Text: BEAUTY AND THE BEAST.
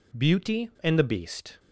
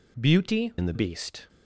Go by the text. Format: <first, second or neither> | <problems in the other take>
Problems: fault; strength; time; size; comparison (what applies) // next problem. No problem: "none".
first | changes voice from "AND" to "THE"; from 0.7 to 0.9 s; 0.2 s long